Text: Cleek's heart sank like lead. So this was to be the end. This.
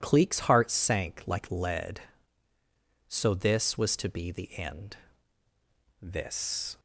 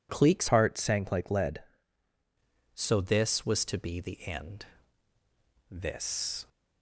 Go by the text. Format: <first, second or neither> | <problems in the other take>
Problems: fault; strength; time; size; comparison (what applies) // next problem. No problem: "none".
first | changes voice from "heart" to "lead"; from 0.4 to 1.6 s; 1.2 s long